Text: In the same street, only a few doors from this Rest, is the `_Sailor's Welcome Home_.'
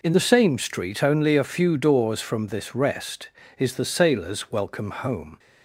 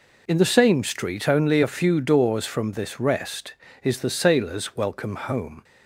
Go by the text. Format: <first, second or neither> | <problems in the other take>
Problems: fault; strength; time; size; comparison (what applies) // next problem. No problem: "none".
neither | none